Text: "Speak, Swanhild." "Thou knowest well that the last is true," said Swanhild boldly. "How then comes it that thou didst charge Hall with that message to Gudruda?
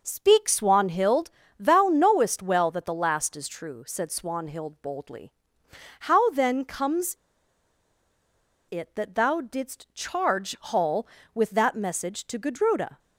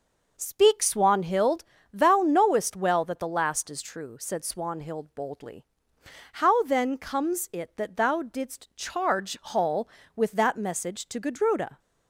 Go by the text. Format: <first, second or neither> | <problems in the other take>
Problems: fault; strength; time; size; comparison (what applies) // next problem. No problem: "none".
second | pauses between "comes" and "it"; strong; at 7.1 s; 1.5 s long